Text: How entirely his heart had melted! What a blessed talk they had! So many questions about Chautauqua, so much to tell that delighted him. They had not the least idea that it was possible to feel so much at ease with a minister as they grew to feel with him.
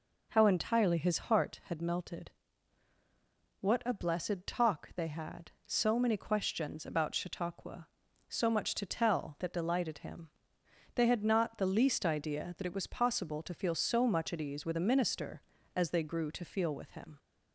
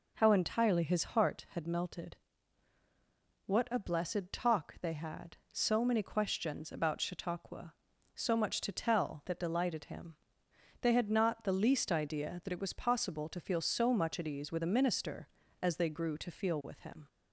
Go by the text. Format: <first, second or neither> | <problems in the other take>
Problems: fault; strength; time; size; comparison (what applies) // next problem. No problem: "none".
neither | none